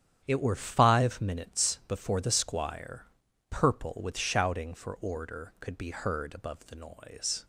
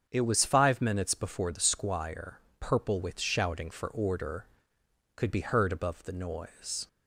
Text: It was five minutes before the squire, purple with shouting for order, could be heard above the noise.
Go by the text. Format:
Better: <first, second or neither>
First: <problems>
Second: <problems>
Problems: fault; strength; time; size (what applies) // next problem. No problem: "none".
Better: second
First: starts louder than the rest; strong; until 1.2 s; 9 dB // says "were" for "was"; at 0.4 s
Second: starts louder than the rest; strong; until 1.1 s; 7.5 dB